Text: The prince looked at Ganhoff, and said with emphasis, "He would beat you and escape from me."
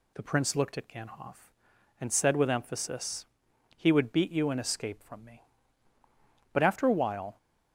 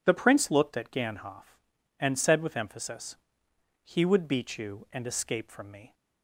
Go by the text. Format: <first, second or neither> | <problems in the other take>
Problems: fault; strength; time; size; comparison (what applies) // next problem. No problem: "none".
second | goes on to say "But after a while"; noticeable; from 6.5 s on; 0.86 s long